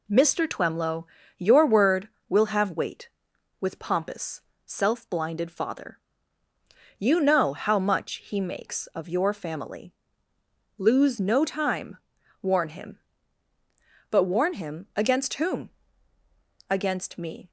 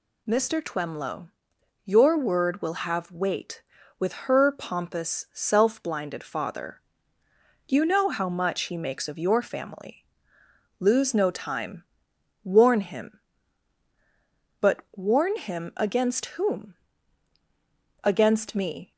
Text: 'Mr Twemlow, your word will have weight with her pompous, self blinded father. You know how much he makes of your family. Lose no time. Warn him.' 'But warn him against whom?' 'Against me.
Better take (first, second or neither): second